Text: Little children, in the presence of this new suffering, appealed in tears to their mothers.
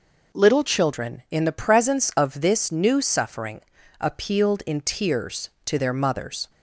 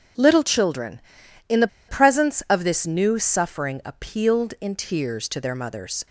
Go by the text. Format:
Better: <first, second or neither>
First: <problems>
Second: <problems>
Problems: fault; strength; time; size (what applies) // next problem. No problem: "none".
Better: first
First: none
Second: pauses between "the" and "presence"; slight; at 1.6 s; 0.21 s long